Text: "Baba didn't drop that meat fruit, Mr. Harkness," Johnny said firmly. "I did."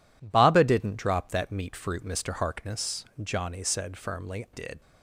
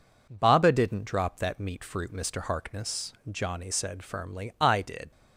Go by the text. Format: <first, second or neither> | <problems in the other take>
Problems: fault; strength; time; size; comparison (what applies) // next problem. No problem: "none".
second | skips "I"; at 4.4 s